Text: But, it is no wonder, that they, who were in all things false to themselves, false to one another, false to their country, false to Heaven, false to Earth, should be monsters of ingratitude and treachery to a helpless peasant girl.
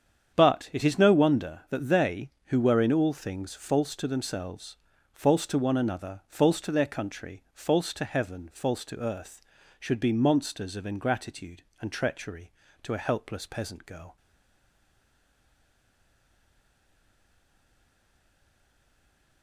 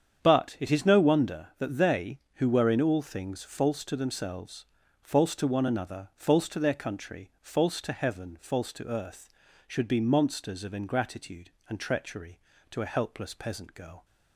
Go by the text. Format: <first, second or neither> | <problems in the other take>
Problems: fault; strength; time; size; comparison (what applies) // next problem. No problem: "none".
second | starts louder than the rest; strong; until 1.3 s; 8 dB; strong in the second // stays silent after the last word; strong; from 14.1 s on; 5.3 s long